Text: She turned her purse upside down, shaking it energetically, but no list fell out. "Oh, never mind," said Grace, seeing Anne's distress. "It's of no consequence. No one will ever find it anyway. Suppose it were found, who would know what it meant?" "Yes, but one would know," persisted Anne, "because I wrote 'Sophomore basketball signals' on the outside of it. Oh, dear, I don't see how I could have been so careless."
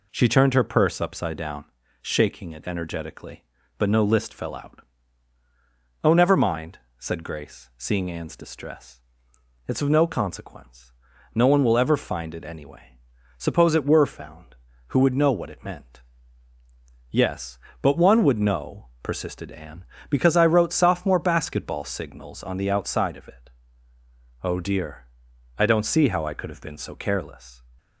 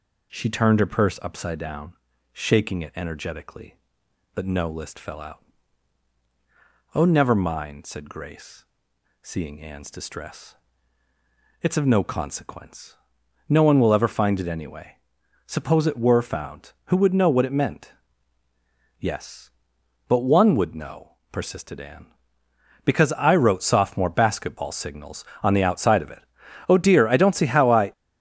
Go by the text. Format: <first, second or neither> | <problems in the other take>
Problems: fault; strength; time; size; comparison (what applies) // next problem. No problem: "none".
first | stops before "could have been so careless"; at 27.9 s